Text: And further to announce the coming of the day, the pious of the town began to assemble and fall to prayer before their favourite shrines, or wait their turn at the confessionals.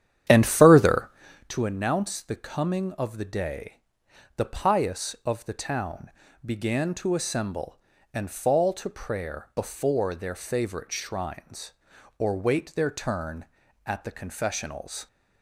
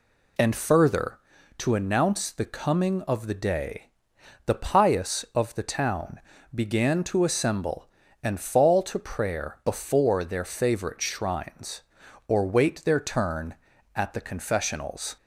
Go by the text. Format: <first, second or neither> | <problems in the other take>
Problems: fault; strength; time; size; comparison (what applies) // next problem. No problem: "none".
second | starts louder than the rest; strong; until 1.5 s; 10 dB // pauses between "town" and "began"; slight; at 6.1 s; 0.34 s long; slight in the second